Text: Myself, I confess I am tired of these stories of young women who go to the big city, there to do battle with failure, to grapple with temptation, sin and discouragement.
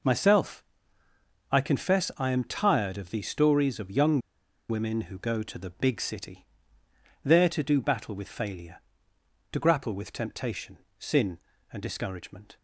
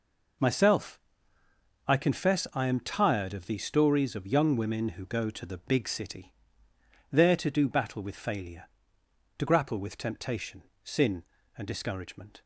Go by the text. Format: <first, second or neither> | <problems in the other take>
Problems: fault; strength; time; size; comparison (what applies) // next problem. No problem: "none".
second | pauses between "young" and "women"; noticeable; at 4.2 s; 0.49 s long